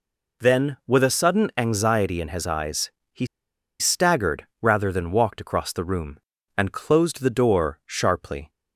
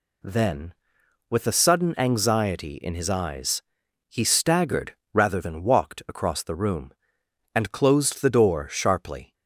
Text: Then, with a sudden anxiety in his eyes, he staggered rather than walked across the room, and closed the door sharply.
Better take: second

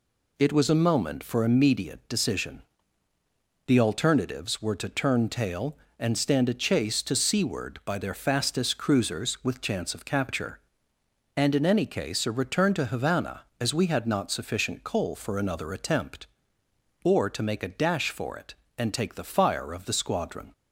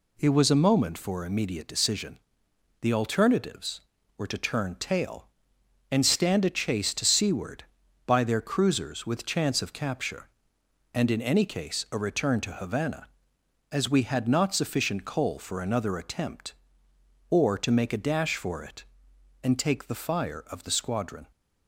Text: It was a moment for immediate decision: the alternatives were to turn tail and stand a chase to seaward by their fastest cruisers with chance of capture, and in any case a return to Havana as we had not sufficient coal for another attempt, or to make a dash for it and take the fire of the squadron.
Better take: first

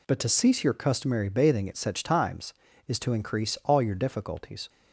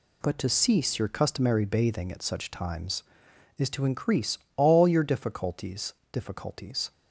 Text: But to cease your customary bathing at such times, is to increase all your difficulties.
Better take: first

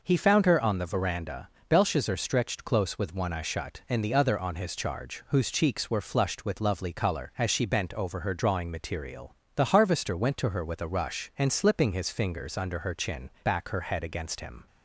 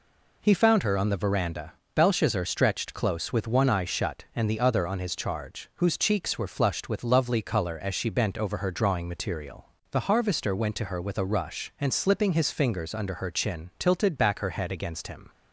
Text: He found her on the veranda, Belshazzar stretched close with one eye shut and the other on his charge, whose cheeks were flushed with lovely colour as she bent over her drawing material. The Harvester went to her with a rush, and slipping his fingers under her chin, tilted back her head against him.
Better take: second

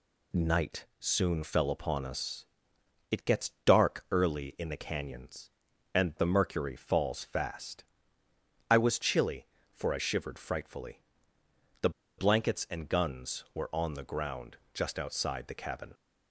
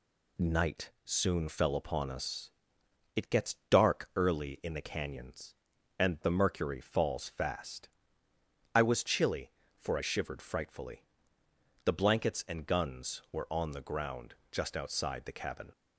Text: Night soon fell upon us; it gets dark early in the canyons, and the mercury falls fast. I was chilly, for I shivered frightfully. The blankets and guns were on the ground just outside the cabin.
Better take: second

